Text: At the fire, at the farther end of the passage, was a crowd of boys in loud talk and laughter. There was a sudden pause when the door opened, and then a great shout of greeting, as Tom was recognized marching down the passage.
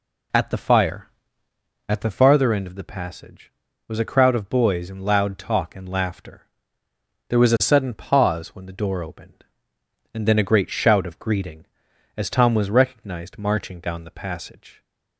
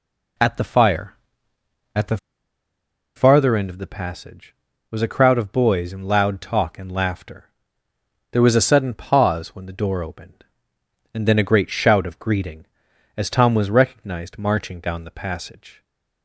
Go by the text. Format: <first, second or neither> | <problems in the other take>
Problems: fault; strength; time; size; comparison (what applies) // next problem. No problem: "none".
first | pauses between "the" and "farther"; at 2.1 s; 0.99 s long